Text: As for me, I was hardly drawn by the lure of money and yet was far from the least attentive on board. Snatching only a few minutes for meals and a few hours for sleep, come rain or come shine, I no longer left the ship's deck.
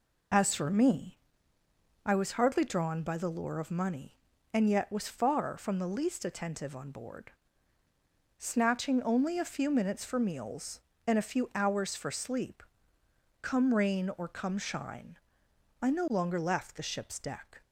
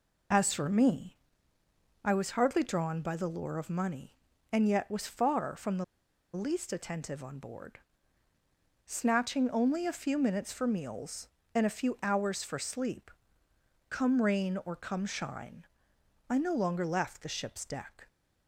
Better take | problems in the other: first | pauses between "the" and "least"; noticeable; at 5.8 s; 0.49 s long

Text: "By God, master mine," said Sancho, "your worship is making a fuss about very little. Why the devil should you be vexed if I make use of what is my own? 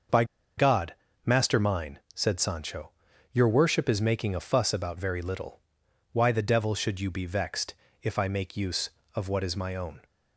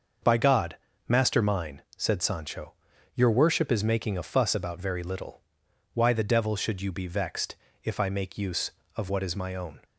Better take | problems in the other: second | starts louder than the rest; until 1.7 s; 6.5 dB; also in the second // pauses between "By" and "God"; slight; at 0.2 s; 0.33 s long // pauses between "vexed" and "if"; slight; at 7.7 s; 0.26 s long; slight in the second

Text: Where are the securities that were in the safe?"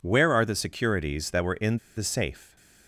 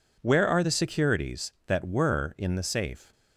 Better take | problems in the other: second | pauses between "in" and "the"; slight; at 1.7 s; 0.20 s long // stays silent after the last word; slight; from 2.3 s on; 0.5 s long

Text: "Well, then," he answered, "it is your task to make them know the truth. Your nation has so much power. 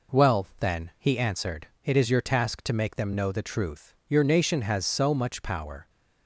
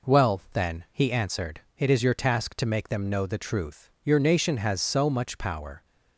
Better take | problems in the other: neither | none

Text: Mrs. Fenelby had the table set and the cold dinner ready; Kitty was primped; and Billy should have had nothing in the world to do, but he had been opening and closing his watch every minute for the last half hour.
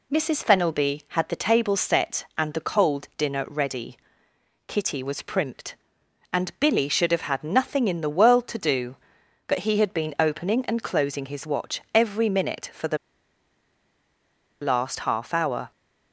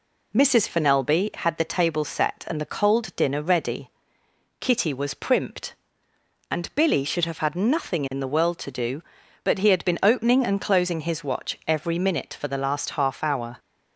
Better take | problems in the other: second | pauses between "the" and "last"; strong; at 12.9 s; 1.6 s long

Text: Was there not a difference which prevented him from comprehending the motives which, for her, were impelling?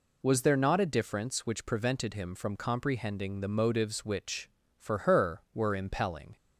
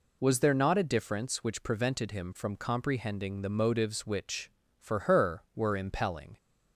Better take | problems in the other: neither | none

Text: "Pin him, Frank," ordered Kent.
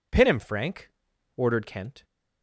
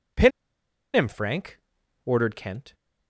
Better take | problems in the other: first | pauses between "Pin" and "him"; noticeable; at 0.3 s; 0.65 s long

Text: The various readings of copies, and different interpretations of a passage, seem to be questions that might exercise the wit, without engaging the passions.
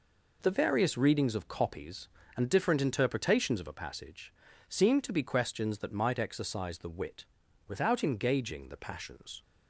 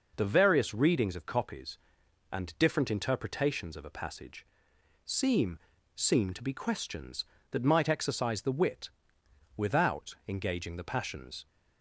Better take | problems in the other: first | says "seem" twice; at 5.9 s

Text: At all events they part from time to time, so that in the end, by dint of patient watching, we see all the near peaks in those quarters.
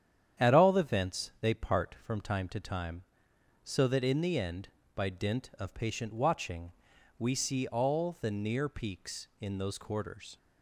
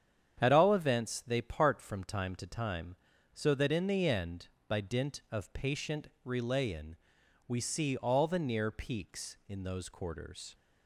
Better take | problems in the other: first | starts louder than the rest; strong; until 1.4 s; 8.5 dB; strong in the first // says "relayin" for "watching"; at 6.2 s

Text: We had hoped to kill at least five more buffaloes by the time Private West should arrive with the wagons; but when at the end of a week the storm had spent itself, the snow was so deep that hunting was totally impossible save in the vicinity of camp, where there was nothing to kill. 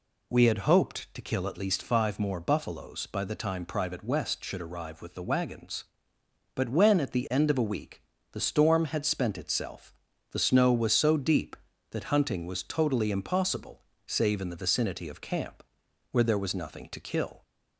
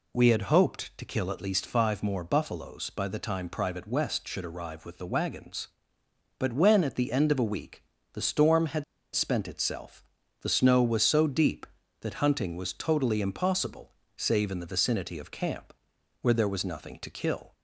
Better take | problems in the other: first | pauses between "week" and "the"; slight; at 7.8 s; 0.30 s long; slight in the first // pauses between "had" and "spent"; slight; at 8.8 s; 0.30 s long // pauses between "impossible" and "save"; slight; at 13.9 s; 0.26 s long; slight in the first

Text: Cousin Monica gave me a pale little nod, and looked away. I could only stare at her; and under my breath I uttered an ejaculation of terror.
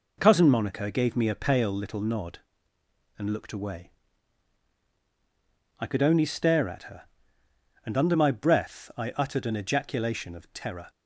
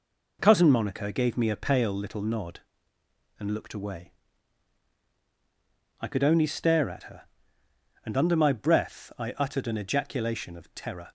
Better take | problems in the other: neither | none

